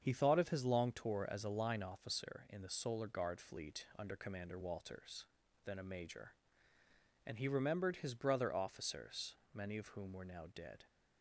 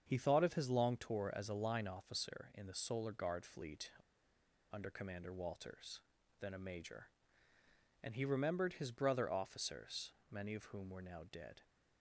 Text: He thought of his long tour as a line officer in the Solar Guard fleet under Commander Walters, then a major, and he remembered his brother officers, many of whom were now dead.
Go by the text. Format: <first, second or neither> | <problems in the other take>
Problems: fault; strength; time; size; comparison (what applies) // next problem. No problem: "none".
first | starts louder than the rest; until 1.0 s; 7 dB; also in the first // pauses between "fleet" and "under"; noticeable; at 3.9 s; 0.79 s long